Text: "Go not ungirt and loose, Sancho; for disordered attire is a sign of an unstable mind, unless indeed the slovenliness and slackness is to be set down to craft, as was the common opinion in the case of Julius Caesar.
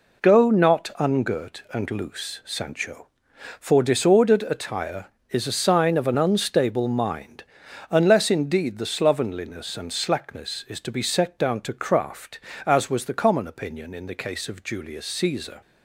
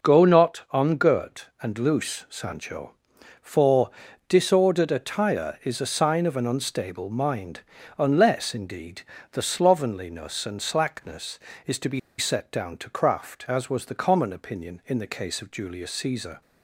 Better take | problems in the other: first | pauses between "for" and "disordered"; at 3.9 s; 0.38 s long // pauses between "indeed" and "the"; slight; at 9.0 s; 0.30 s long // pauses between "be" and "set"; slight; at 11.9 s; 0.19 s long

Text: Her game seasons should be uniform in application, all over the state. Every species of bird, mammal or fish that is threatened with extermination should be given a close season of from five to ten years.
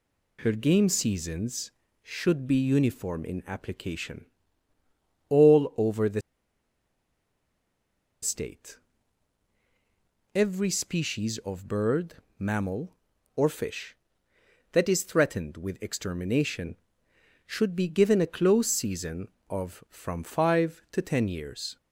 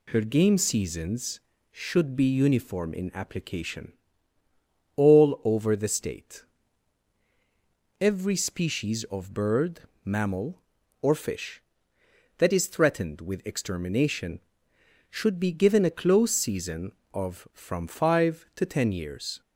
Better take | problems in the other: second | pauses between "the" and "state"; strong; at 6.2 s; 2.0 s long

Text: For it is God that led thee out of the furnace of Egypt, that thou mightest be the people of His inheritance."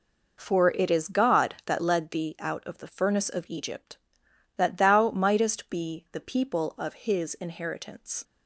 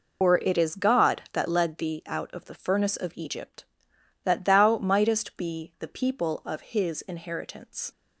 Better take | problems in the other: first | loses the start of "For"; at 0.2 s; 160 ms

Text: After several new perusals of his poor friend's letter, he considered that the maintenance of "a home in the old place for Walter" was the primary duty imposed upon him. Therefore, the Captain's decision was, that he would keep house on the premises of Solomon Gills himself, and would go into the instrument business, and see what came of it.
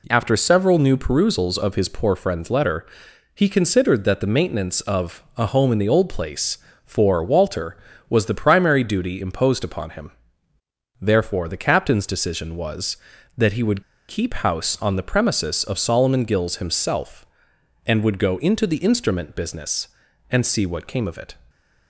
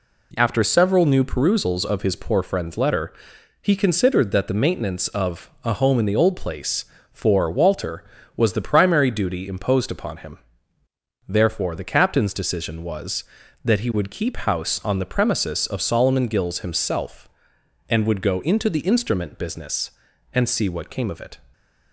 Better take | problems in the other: second | pauses between "would" and "keep"; slight; at 13.8 s; 0.27 s long

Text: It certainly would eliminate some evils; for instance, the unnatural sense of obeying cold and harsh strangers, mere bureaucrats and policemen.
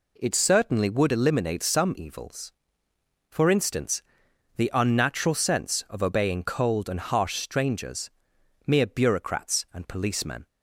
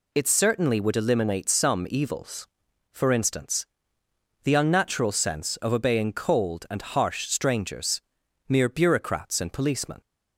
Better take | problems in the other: neither | none

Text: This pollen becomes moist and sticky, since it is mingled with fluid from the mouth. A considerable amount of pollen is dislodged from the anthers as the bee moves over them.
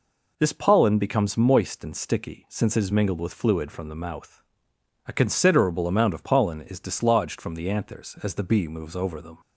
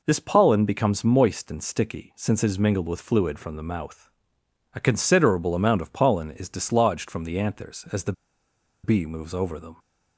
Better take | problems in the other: first | pauses between "the" and "bee"; noticeable; at 8.1 s; 0.71 s long

